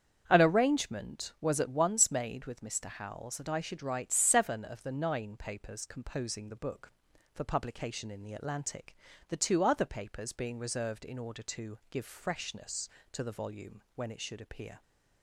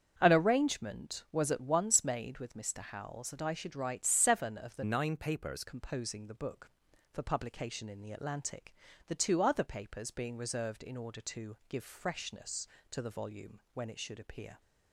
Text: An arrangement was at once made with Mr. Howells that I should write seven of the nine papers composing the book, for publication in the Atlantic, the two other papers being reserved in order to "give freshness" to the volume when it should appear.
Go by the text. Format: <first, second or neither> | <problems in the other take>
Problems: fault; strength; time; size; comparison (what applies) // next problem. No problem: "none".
first | starts louder than the rest; strong; until 1.1 s; 7.5 dB; strong in the first // changes voice from "nine" to "papers"; from 4.8 to 5.6 s; 0.8 s long